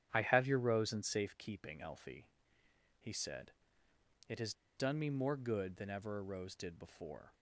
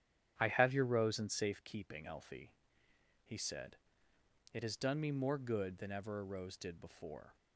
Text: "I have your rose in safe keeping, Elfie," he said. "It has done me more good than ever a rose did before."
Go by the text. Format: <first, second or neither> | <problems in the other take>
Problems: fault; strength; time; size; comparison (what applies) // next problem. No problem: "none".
second | starts louder than the rest; strong; until 1.1 s; 10 dB; strong in the second // pauses between "has" and "done"; slight; at 4.5 s; 0.24 s long